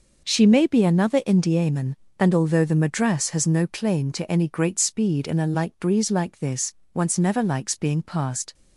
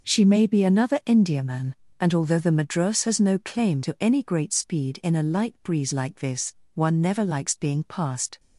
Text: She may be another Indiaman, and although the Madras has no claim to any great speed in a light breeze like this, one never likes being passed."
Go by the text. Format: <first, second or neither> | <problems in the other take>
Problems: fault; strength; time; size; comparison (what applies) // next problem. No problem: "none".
second | says "once" for "one"; at 6.9 s